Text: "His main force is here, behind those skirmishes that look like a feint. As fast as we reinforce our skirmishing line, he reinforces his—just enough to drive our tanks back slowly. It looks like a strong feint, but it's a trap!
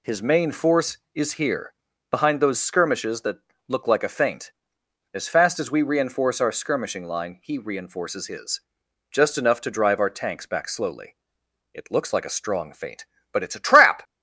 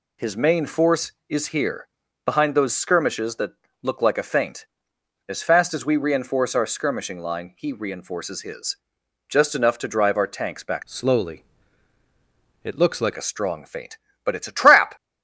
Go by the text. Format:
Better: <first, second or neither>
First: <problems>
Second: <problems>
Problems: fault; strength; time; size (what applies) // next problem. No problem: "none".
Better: first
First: pauses between "that" and "look"; slight; at 3.3 s; 0.28 s long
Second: pauses between "that" and "look"; slight; at 3.5 s; 0.28 s long // changes voice from "slowly" to "like"; from 10.8 to 13.1 s; 2.3 s long